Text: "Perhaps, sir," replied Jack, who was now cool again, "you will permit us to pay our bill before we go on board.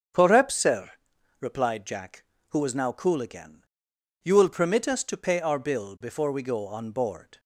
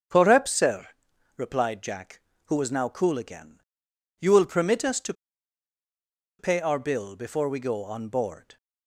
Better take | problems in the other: first | starts louder than the rest; strong; until 1.5 s; 7.5 dB; strong in the first // pauses between "to" and "pay"; strong; at 5.1 s; 1.2 s long

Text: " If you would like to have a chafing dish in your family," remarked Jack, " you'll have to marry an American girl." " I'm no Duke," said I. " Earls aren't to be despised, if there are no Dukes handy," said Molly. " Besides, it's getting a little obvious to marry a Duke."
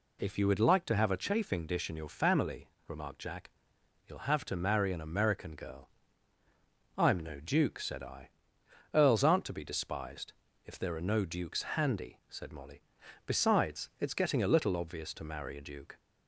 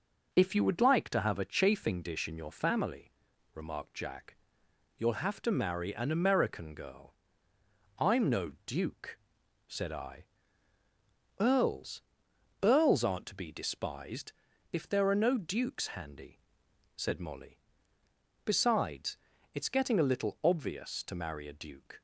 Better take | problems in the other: first | starts louder than the rest; until 1.3 s; 6 dB // says "Earls" twice; at 12.6 s

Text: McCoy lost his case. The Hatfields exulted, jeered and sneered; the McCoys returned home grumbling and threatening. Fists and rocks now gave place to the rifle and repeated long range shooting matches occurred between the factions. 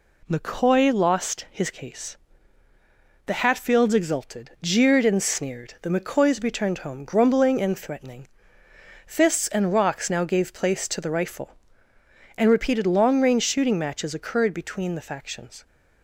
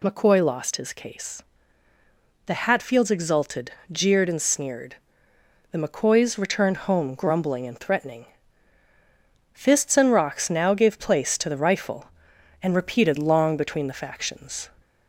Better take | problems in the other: first | skips "range shooting matches occurred"; at 13.5 s

